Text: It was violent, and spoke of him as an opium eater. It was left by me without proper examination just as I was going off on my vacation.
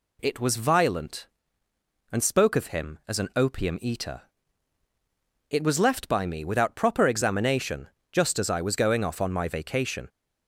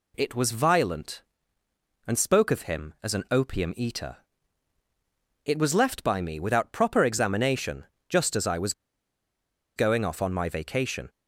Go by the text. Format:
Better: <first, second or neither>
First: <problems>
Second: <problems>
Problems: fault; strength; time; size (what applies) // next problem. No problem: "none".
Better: first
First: pauses between "examination" and "just"; slight; at 7.8 s; 0.22 s long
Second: pauses between "examination" and "just"; slight; at 7.8 s; 0.22 s long // pauses between "was" and "going"; at 8.7 s; 1.0 s long